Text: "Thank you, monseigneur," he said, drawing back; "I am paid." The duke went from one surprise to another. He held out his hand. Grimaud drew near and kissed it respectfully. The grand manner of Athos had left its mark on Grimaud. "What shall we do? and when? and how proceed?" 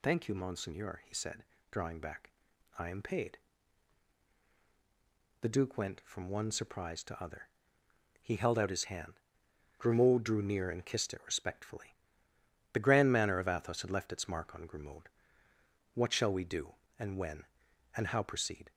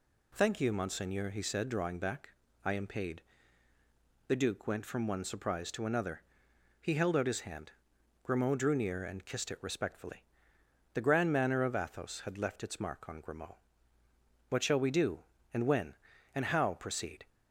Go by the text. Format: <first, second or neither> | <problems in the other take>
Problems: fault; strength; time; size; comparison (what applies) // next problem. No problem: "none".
second | says "other" for "another"; at 7.2 s